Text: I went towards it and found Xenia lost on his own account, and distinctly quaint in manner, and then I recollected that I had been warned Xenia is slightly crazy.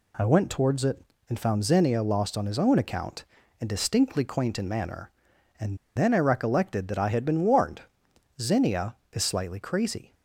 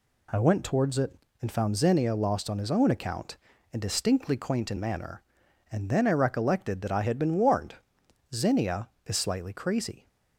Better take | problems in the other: second | pauses between "and" and "then"; slight; at 5.7 s; 0.18 s long // pauses between "warned" and "Xenia"; noticeable; at 7.8 s; 0.58 s long; noticeable in the second

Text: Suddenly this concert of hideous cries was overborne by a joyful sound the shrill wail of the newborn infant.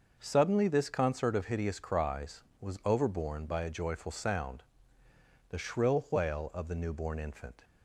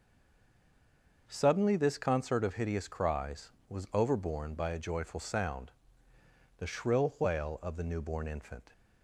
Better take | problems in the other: first | stays silent before the first word; noticeable; until 1.2 s; 1.2 s long // starts louder than the rest; noticeable; until 2.2 s; 6 dB // pauses between "sound" and "the"; noticeable; at 5.7 s; 0.86 s long; noticeable in the first

